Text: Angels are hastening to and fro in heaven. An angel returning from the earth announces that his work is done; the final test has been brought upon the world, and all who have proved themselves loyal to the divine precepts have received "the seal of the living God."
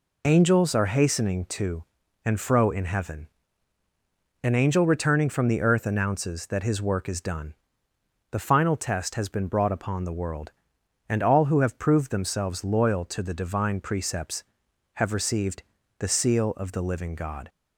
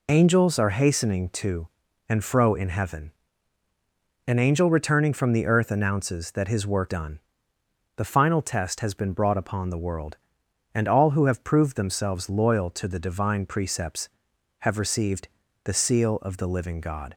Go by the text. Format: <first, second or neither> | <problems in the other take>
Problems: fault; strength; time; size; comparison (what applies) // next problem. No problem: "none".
first | skips "is"; at 6.8 s // pauses between "received" and "the"; slight; at 15.2 s; 0.36 s long; slight in the first